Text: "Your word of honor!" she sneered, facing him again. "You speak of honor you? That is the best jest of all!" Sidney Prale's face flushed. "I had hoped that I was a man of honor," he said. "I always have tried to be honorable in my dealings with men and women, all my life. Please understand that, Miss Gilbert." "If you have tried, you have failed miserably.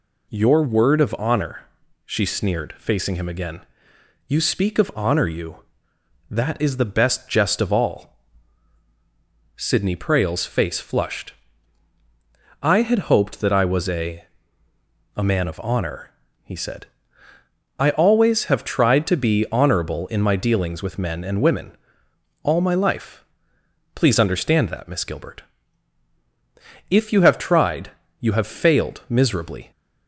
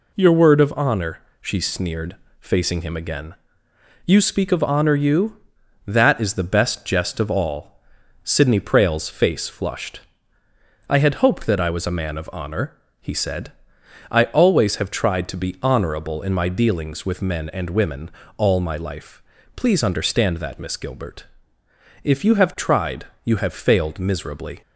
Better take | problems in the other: second | says "a" twice; at 15.1 s

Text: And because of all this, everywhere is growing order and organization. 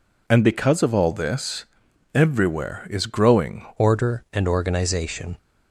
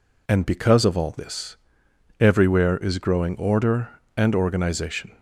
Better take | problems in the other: second | changes voice at "order"; from 3.7 s on; 1.6 s long

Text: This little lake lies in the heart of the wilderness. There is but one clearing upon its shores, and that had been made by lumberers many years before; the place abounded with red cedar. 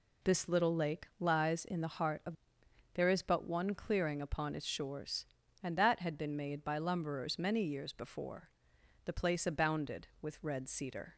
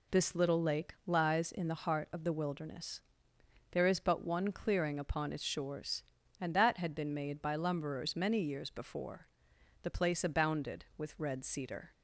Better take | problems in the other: second | skips "the wilderness"; at 2.6 s

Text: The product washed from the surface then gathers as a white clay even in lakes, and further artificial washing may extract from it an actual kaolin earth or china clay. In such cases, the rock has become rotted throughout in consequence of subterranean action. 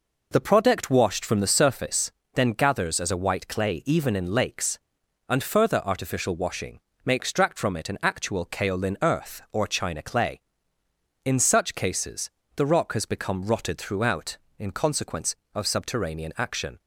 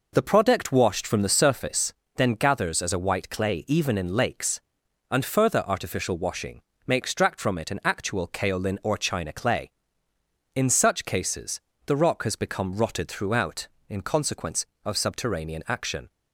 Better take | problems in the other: first | pauses between "surface" and "then"; slight; at 1.9 s; 0.24 s long; slight in the first // pauses between "washing" and "may"; slight; at 6.6 s; 0.24 s long; slight in the first // skips "earth"; at 8.8 s

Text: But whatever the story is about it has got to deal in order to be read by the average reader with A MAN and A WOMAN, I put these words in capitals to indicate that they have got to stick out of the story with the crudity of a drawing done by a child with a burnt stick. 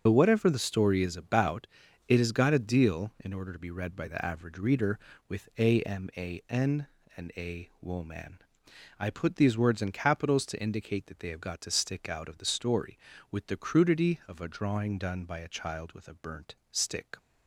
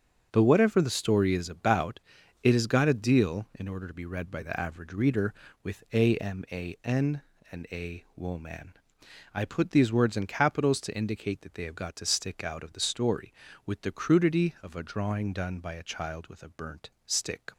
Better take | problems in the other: second | loses the start of "But"; at 0.0 s; 55 ms // pauses between "about" and "it"; at 1.6 s; 0.40 s long; also in the second // pauses between "burnt" and "stick"; slight; at 16.5 s; 0.16 s long; slight in the second

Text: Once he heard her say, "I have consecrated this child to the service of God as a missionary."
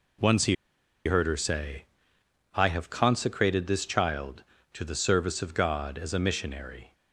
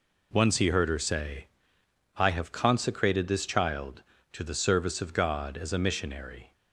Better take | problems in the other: second | pauses between "he" and "heard"; noticeable; at 0.5 s; 0.50 s long

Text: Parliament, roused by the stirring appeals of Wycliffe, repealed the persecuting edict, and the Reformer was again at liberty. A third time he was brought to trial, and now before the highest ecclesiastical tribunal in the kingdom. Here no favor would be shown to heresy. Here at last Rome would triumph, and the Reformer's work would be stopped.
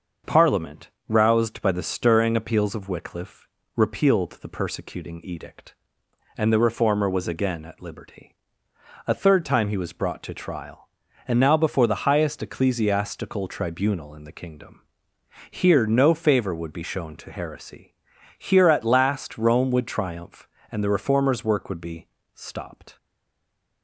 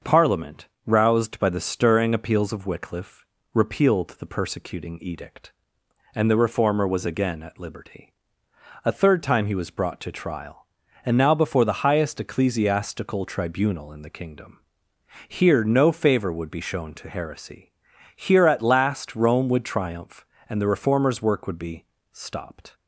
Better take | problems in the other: second | starts louder than the rest; until 1.4 s; 6 dB; also in the second // pauses between "be" and "stopped"; slight; at 22.0 s; 0.26 s long; slight in the second // stays silent after the last word; slight; from 22.9 s on; 0.9 s long

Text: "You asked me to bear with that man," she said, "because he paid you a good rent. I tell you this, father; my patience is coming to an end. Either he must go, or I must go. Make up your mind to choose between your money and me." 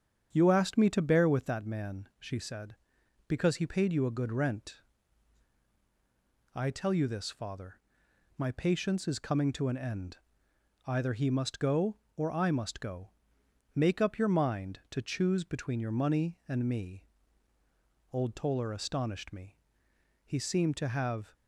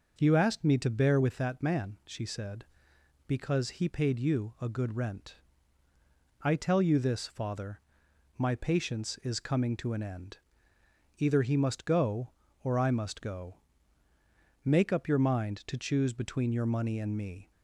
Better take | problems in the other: second | starts louder than the rest; strong; until 1.3 s; 8 dB // goes on to say "Old Toller astonished me He seemed to have"; strong; from 18.1 s on; 3.2 s long

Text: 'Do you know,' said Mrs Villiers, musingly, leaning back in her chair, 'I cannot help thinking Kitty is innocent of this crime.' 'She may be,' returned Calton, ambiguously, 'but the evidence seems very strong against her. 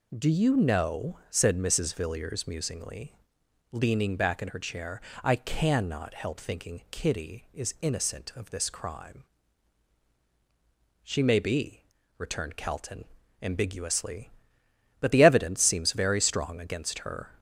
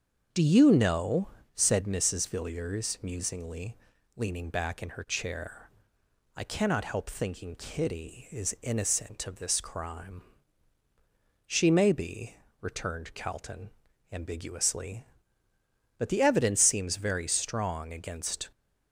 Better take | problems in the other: first | starts louder than the rest; until 1.5 s; 7 dB // stops before "her"; at 18.5 s

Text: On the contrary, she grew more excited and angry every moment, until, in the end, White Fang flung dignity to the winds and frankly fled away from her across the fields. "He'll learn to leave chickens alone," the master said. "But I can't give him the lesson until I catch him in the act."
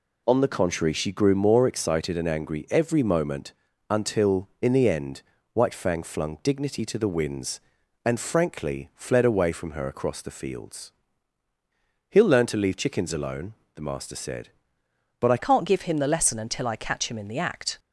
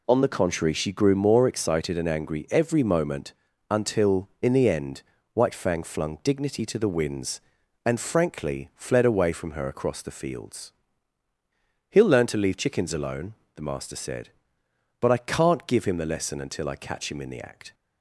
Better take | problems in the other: second | changes voice at "can't"; from 15.3 s on; 2.4 s long

